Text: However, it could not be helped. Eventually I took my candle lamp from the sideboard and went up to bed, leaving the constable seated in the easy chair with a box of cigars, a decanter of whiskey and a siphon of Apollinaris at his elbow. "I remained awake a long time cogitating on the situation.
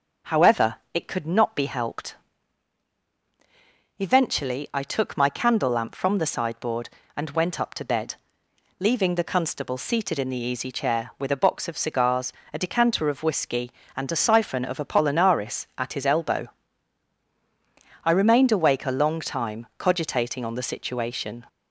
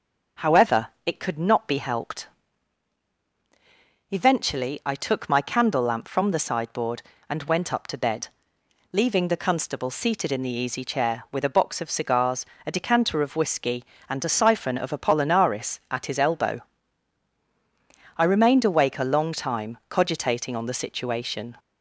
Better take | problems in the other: neither | starts louder than the rest; the same in both

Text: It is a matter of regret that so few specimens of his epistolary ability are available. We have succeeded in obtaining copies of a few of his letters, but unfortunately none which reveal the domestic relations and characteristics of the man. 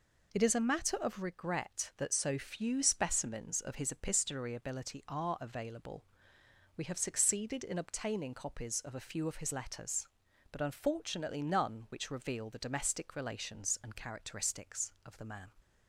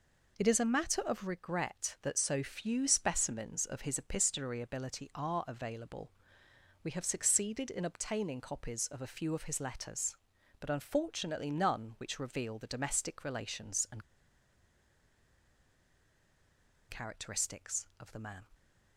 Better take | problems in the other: first | pauses between "and" and "characteristics"; strong; at 14.0 s; 2.8 s long

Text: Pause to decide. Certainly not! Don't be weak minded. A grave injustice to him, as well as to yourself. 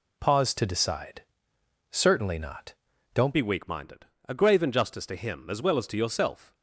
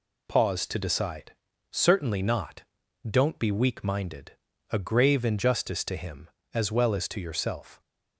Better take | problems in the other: second | changes voice at "be"; from 3.3 s on; 3.2 s long

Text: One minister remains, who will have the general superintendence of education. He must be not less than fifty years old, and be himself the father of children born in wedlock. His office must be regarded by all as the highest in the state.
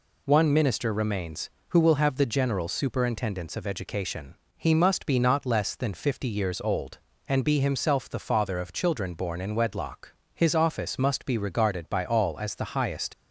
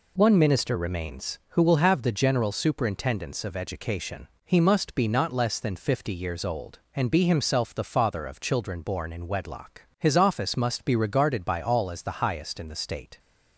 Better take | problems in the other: second | stops before "in the state"; at 13.1 s

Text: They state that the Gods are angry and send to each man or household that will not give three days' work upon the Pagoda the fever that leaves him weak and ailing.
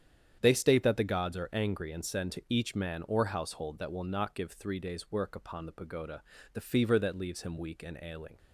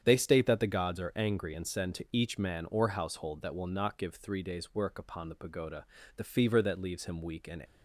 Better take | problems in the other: first | starts louder than the rest; strong; until 1.0 s; 8.5 dB; strong in the first // pauses between "Pagoda" and "the"; slight; at 5.8 s; 0.32 s long; slight in the first // stops before "ailing"; at 7.6 s

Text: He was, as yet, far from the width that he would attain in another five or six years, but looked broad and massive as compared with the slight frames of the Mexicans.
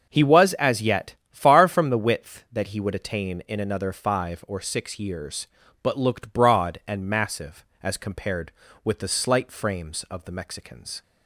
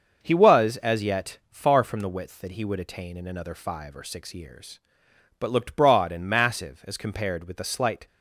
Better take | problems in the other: first | starts louder than the rest; until 1.2 s; 6.5 dB; also in the first // stops before "frames of the Mexicans"; at 8.0 s

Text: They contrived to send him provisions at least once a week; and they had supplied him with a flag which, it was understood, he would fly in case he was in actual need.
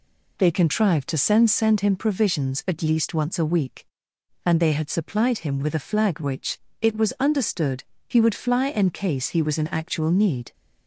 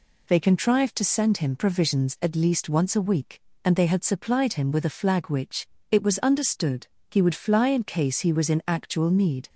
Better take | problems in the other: second | says "send" twice; at 1.5 s

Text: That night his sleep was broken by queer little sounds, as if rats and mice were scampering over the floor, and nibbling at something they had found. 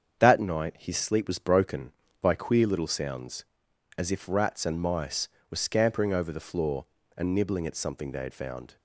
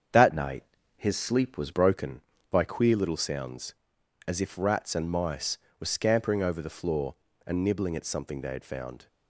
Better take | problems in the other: first | starts louder than the rest; strong; until 1.4 s; 7.5 dB; strong in the first // changes voice from "night" to "was"; from 0.3 to 1.7 s; 1.4 s long // pauses between "night" and "his"; slight; at 0.6 s; 0.32 s long

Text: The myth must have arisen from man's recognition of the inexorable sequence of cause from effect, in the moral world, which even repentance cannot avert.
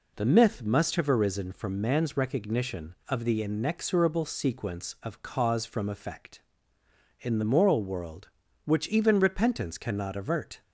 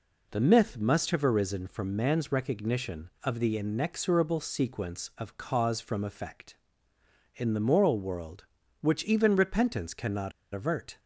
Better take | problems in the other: first | pauses between "cannot" and "avert"; slight; at 10.3 s; 0.23 s long

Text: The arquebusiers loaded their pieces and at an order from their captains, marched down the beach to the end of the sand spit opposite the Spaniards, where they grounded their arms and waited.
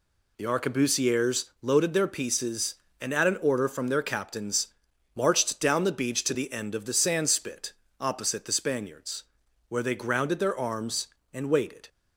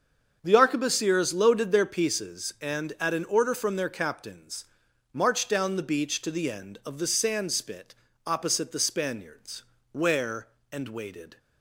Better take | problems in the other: first | starts louder than the rest; until 1.4 s; 7 dB // pauses between "spit" and "opposite"; slight; at 7.9 s; 0.32 s long; slight in the first // skips "they grounded their arms"; at 10.5 s

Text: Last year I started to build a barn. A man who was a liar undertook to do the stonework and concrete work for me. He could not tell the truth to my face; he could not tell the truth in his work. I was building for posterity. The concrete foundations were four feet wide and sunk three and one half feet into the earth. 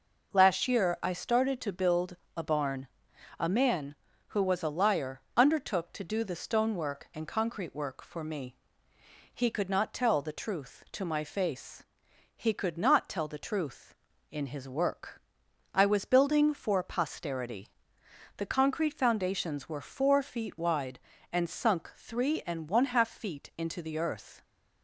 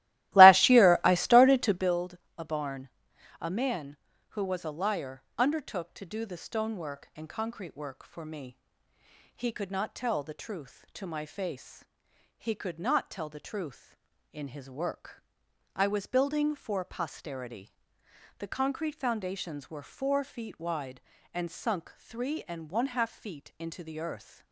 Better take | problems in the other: first | starts louder than the rest; strong; until 2.0 s; 16.5 dB // pauses between "build" and "a"; slight; at 2.1 s; 0.22 s long; slight in the first

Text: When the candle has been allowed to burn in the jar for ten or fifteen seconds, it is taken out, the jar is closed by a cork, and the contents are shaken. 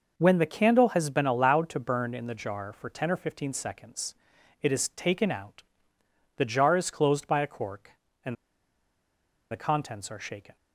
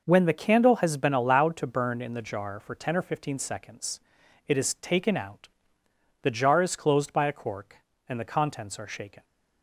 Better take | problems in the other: second | pauses between "and" and "the"; at 8.3 s; 1.1 s long

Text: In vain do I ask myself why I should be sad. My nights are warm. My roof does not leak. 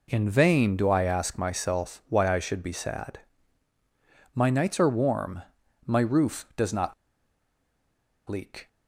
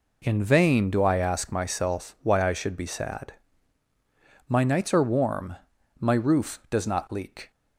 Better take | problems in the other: second | pauses between "not" and "leak"; strong; at 6.9 s; 1.3 s long

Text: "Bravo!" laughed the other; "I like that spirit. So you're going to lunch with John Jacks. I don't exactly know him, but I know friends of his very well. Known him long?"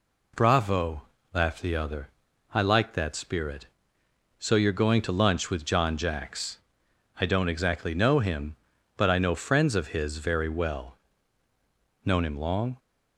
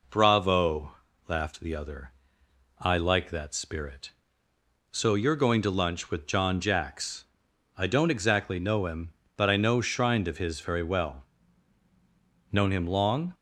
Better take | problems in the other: first | says "shrined" for "friends"; at 9.8 s

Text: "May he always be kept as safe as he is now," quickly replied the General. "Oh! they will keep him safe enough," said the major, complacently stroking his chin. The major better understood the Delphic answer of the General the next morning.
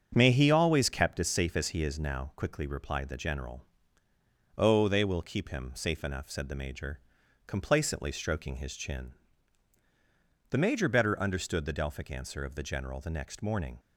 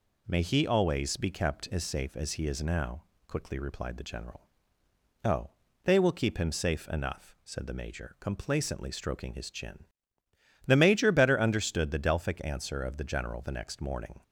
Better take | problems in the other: second | starts louder than the rest; strong; until 1.1 s; 7.5 dB // skips "be"; at 0.8 s

